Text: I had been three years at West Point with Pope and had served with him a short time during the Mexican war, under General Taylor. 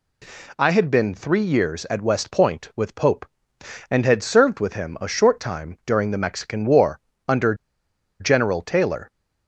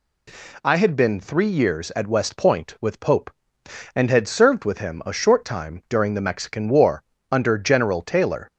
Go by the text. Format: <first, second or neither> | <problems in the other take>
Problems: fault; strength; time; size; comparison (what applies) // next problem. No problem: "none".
second | pauses between "under" and "General"; noticeable; at 7.5 s; 0.65 s long